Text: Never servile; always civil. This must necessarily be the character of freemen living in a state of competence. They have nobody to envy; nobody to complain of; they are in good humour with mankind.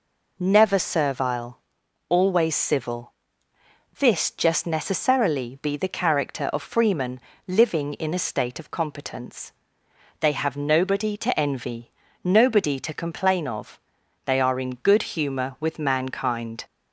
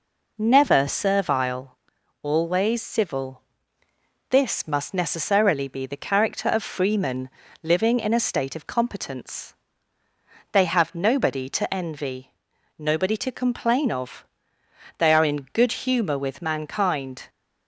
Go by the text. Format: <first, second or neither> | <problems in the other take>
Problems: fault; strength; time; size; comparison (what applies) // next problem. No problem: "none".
second | says "just" for "must"; at 4.2 s // pauses between "freemen" and "living"; slight; at 7.1 s; 0.28 s long; slight in the second